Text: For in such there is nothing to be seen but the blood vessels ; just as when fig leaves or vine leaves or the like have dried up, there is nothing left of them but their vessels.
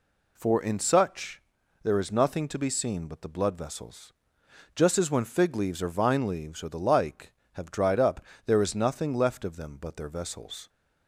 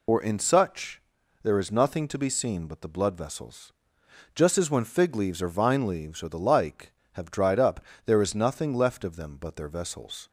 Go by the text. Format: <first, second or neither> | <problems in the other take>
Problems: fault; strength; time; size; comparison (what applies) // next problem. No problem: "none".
first | loses the start of "For"; at 0.0 s; 125 ms // pauses between "such" and "there"; at 0.9 s; 0.42 s long; also in the first